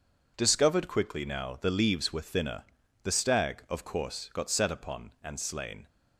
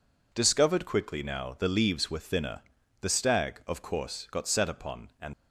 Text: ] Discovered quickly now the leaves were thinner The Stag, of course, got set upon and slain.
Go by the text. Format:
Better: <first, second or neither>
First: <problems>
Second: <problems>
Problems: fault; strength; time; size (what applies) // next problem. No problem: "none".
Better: first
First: pauses between "thinner" and "The"; at 2.6 s; 0.40 s long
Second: pauses between "thinner" and "The"; at 2.6 s; 0.40 s long // stops before "slain"; at 5.3 s